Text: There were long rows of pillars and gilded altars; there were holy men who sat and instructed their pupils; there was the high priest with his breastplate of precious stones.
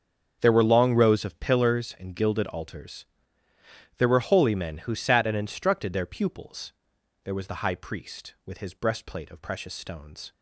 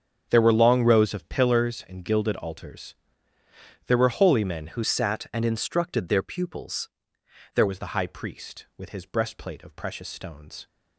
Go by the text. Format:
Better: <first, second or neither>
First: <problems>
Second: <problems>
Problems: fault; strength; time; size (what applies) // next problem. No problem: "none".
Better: first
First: starts louder than the rest; strong; until 1.4 s; 7.5 dB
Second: starts louder than the rest; strong; until 1.3 s; 8 dB // changes voice from "sat" to "there"; from 4.8 to 7.6 s; 2.8 s long